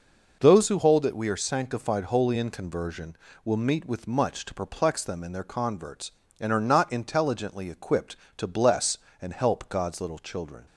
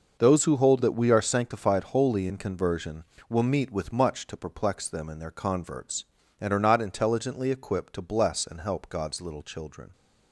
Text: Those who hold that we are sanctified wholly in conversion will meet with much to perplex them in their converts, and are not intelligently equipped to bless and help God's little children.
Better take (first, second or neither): neither